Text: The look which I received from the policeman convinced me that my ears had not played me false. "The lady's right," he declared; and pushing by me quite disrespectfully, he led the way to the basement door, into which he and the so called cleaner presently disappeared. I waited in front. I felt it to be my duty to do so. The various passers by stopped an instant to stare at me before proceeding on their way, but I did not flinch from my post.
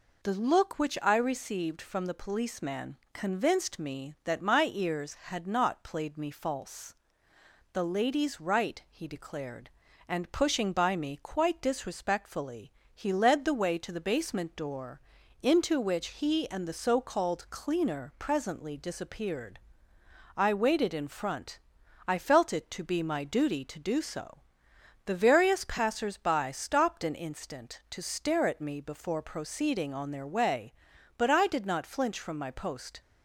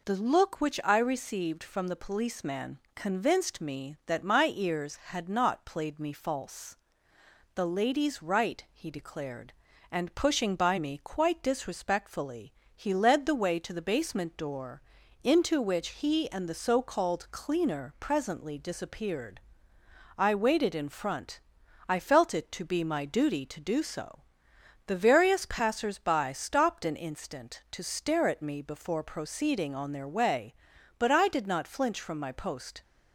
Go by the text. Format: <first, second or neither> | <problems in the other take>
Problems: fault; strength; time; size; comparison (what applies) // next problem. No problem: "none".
neither | pauses between "policeman" and "convinced"; slight; the same in both